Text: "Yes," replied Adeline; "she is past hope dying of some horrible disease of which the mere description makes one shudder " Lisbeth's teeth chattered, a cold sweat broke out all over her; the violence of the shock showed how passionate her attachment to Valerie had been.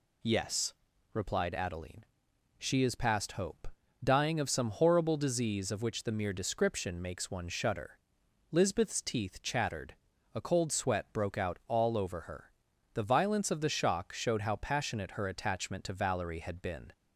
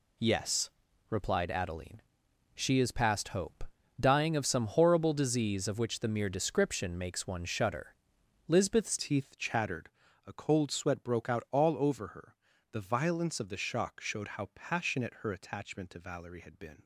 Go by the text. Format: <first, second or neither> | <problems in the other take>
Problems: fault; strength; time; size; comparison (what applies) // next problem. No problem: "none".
first | pauses between "hope" and "dying"; slight; at 3.6 s; 0.34 s long; slight in the first // changes voice at "teeth"; from 8.9 s on; 7.9 s long